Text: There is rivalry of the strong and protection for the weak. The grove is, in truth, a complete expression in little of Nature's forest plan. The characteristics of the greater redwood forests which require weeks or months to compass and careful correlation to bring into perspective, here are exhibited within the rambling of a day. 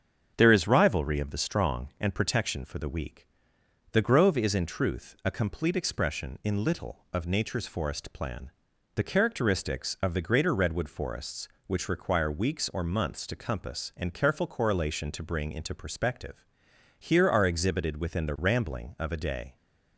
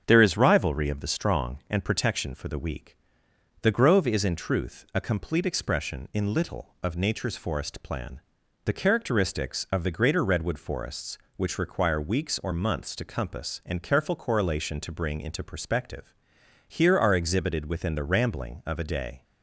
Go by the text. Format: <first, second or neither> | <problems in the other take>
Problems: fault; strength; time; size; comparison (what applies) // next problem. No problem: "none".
neither | starts louder than the rest; the same in both